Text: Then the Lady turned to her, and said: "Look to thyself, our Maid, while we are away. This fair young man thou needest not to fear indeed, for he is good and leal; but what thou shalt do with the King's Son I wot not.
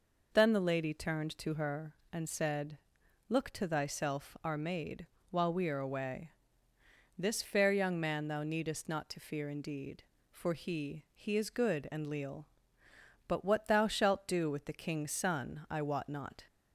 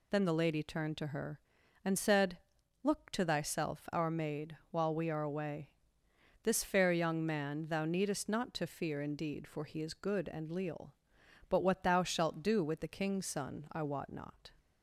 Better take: second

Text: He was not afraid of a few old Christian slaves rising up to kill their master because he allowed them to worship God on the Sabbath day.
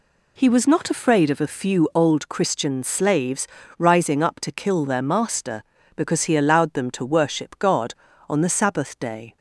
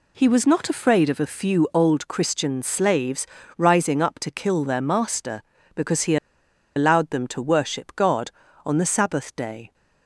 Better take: first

